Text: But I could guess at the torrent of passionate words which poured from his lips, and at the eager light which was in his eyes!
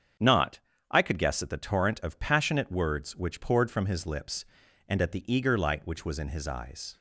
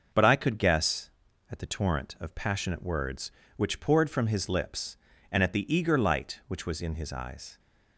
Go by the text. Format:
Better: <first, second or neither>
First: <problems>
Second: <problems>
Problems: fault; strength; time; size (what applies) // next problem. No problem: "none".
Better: second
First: starts louder than the rest; strong; until 1.5 s; 7.5 dB // says "Not" for "But"; at 0.1 s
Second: starts louder than the rest; noticeable; until 1.5 s; 6 dB